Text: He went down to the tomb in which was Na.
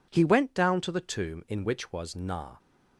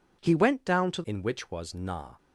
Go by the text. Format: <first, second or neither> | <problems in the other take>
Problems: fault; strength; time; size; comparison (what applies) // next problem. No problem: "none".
first | skips "the tomb"; at 1.0 s